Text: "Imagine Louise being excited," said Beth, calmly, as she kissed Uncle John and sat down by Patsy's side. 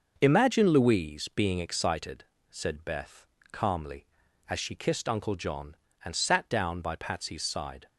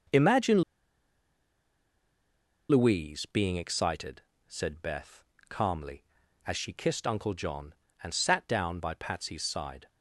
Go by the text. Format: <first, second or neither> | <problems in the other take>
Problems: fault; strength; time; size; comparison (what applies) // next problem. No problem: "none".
first | starts louder than the rest; noticeable; until 3.2 s; 6 dB; noticeable in the first // pauses between "Imagine" and "Louise"; strong; at 0.6 s; 2.0 s long